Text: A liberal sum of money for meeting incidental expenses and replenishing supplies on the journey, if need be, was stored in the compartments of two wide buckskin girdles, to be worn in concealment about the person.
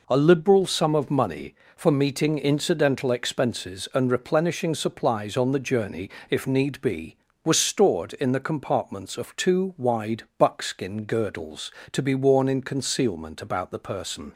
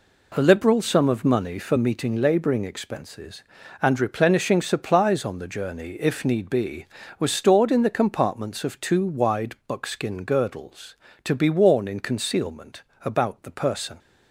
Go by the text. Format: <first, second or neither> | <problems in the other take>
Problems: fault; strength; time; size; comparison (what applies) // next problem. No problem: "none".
first | says "labouring" for "incidental"; at 2.1 s // pauses between "concealment" and "about"; slight; at 12.8 s; 0.24 s long